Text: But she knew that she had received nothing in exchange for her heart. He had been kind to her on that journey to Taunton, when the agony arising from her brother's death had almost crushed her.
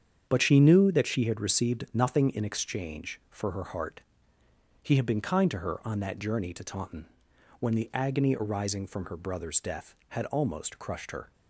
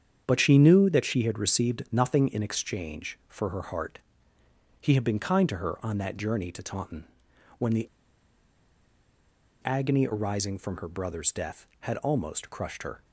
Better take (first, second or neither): first